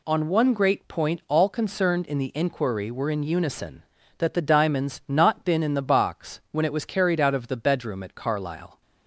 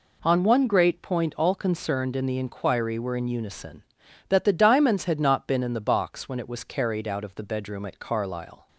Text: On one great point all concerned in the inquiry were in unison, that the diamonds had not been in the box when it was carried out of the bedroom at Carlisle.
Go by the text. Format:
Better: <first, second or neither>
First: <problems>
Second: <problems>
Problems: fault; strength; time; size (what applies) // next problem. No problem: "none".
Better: second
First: skips "had"; at 5.0 s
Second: none